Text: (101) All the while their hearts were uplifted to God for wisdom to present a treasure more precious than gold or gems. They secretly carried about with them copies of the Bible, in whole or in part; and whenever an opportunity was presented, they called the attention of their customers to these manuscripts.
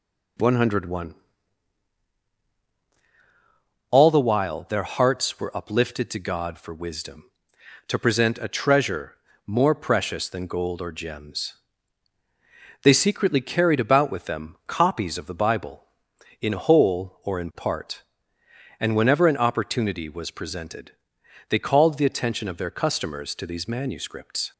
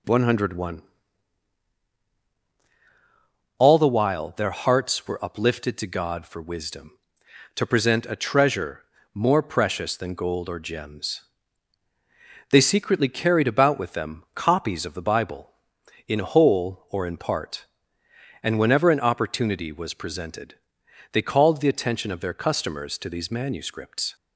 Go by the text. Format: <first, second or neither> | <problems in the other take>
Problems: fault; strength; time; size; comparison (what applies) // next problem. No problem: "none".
neither | pauses between "treasure" and "more"; slight; the same in both